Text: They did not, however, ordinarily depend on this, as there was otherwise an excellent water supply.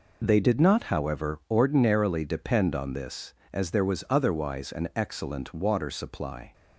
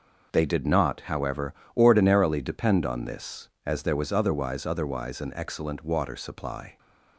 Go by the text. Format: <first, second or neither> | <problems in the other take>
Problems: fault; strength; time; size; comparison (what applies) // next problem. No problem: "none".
first | says "otherwise" twice; at 4.6 s